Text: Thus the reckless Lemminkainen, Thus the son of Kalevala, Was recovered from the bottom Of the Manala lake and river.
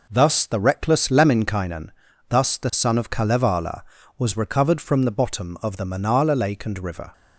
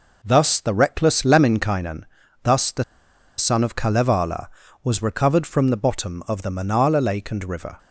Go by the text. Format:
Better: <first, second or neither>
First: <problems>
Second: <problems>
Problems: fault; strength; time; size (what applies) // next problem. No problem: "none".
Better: first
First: none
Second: pauses between "the" and "son"; noticeable; at 2.8 s; 0.54 s long